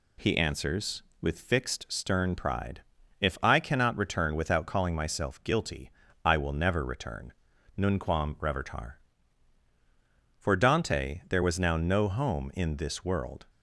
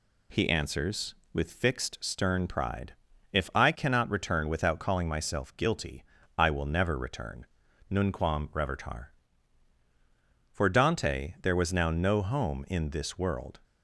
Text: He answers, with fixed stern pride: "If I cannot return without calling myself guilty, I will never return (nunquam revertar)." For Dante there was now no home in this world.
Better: neither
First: none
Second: none

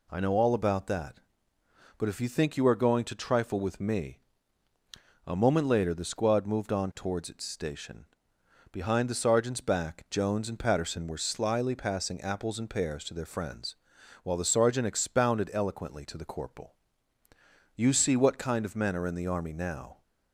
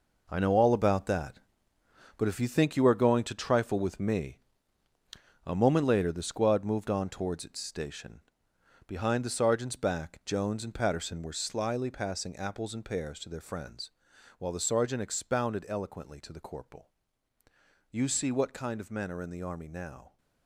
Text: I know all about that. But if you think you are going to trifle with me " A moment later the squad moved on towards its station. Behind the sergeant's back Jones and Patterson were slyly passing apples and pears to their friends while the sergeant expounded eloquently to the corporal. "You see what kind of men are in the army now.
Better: first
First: pauses between "friends" and "while"; noticeable; at 13.7 s; 0.48 s long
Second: gets quieter; strong; throughout; 8 dB // pauses between "friends" and "while"; noticeable; at 13.9 s; 0.48 s long

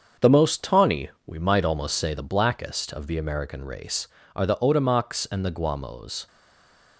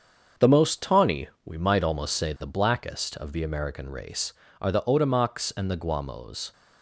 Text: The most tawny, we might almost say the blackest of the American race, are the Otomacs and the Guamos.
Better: second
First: starts louder than the rest; until 1.3 s; 7 dB // stays silent after the last word; slight; from 6.2 s on; 0.7 s long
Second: starts louder than the rest; until 1.5 s; 7 dB

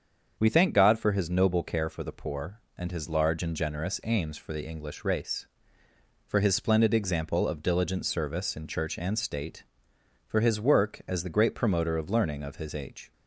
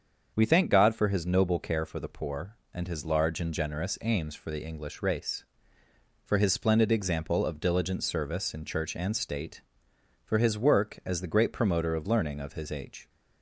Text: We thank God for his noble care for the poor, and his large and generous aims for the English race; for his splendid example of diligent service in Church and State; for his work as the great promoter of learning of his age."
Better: neither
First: starts louder than the rest; until 1.4 s; 7 dB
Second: starts louder than the rest; until 1.3 s; 7 dB

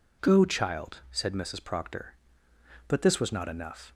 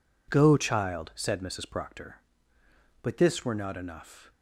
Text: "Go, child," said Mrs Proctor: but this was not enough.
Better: first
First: none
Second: says "were" for "was"; at 3.4 s

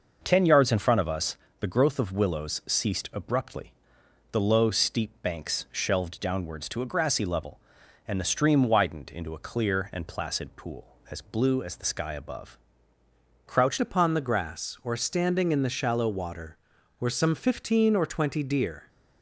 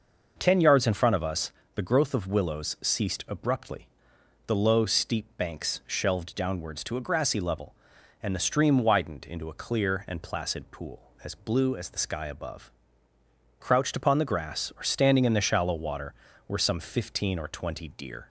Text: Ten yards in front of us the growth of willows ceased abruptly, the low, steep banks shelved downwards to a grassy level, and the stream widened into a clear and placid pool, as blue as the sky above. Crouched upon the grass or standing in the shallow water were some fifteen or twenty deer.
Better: second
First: pauses between "us" and "the"; slight; at 1.3 s; 0.22 s long // changes voice at "upon"; from 13.7 s on; 5.1 s long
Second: pauses between "us" and "the"; slight; at 1.5 s; 0.22 s long

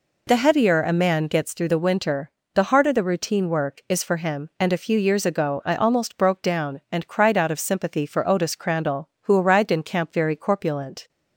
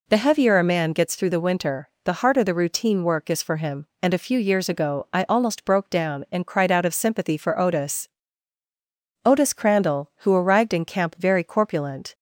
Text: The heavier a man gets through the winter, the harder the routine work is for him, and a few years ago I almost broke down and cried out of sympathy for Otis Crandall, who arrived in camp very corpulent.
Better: first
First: none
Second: says "Otis" twice; at 9.2 s

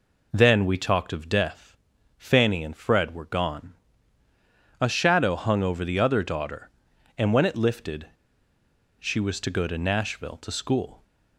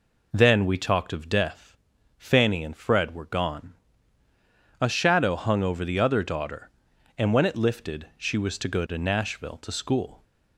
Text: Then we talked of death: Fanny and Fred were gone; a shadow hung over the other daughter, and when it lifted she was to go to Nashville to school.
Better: second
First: pauses between "lifted" and "she"; noticeable; at 8.0 s; 0.92 s long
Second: none

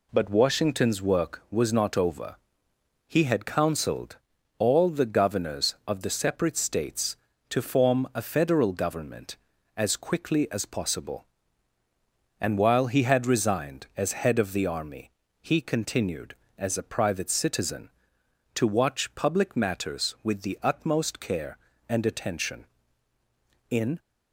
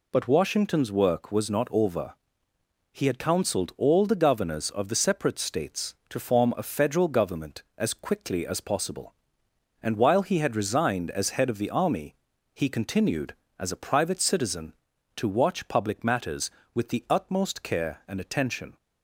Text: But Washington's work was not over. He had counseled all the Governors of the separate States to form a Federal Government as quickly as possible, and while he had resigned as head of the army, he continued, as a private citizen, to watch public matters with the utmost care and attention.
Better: second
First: pauses between "counseled" and "all"; at 4.1 s; 0.40 s long // goes on to say "In"; slight; from 23.6 s on; 0.30 s long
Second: none

